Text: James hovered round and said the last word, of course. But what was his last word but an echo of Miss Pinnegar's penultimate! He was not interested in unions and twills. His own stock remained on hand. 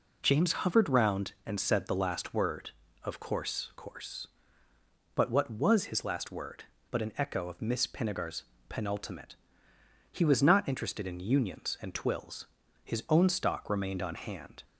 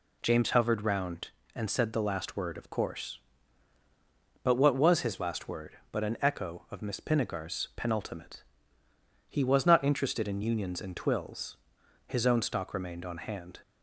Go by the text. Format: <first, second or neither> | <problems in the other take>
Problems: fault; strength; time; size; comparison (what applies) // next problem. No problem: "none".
second | says "course" twice; at 3.7 s // pauses between "Pinnegar's" and "penultimate"; slight; at 8.4 s; 0.26 s long